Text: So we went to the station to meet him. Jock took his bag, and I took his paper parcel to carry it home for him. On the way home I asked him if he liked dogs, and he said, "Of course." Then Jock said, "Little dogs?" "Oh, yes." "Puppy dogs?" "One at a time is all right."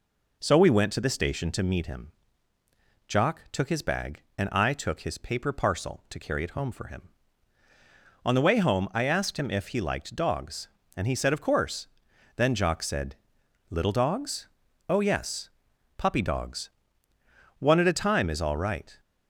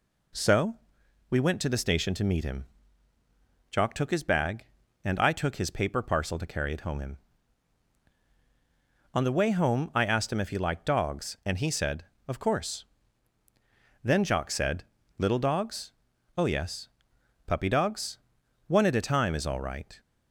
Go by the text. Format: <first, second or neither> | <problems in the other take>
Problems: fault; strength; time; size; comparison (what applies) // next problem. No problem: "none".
first | pauses between "So" and "we"; noticeable; at 0.7 s; 0.56 s long // skips "for"; at 6.9 s